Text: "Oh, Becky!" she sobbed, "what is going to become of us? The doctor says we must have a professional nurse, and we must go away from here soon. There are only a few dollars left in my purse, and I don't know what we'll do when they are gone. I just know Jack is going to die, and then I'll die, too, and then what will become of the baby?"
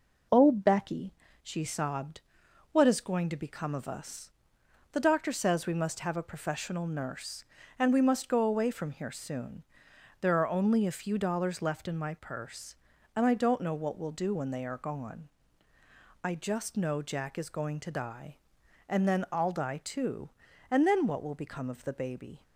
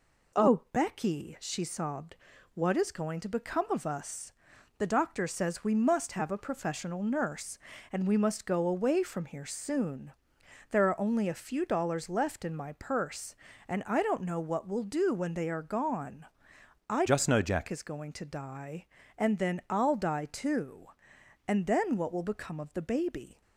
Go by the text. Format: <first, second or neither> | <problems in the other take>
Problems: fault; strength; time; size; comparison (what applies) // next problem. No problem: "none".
first | changes voice from "just" to "Jack"; from 17.0 to 17.6 s; 0.6 s long